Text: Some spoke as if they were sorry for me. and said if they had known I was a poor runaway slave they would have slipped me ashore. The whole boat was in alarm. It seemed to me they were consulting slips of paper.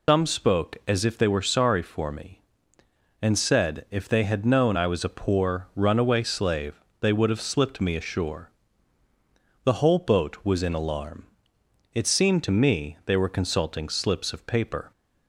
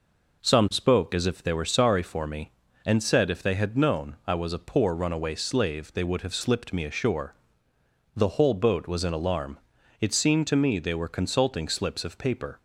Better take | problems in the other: second | loses the start of "Some"; at 0.0 s; 145 ms // pauses between "slave" and "they"; slight; at 6.7 s; 0.20 s long

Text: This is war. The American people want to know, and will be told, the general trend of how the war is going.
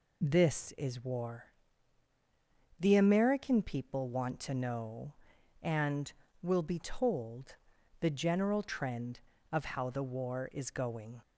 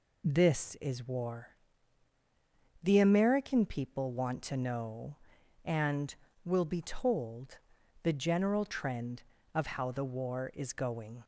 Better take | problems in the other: neither | none

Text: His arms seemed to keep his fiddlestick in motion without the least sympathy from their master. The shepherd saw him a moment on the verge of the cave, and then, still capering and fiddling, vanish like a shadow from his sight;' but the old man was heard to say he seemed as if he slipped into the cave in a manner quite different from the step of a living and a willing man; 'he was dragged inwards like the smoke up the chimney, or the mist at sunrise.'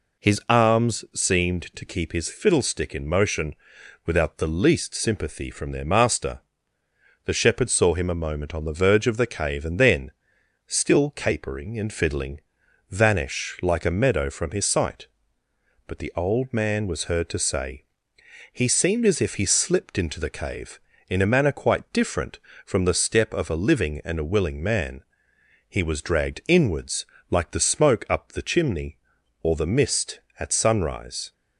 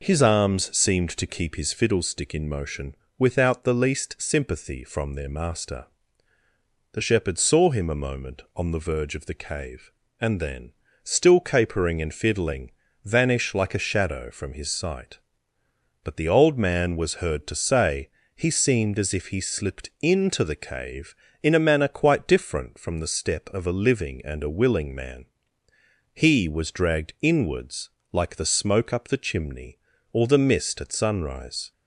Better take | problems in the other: second | pauses between "motion" and "without"; noticeable; at 3.5 s; 0.52 s long; slight in the second // says "meadow" for "shadow"; at 13.9 s // pauses between "say" and "he"; noticeable; at 17.8 s; 0.68 s long; slight in the second // pauses between "inwards" and "like"; slight; at 27.0 s; 0.24 s long; slight in the second

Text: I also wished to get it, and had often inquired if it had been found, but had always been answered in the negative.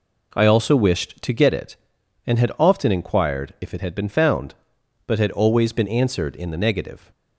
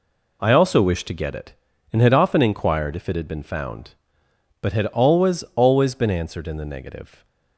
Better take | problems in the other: first | says "always" twice; at 5.5 s

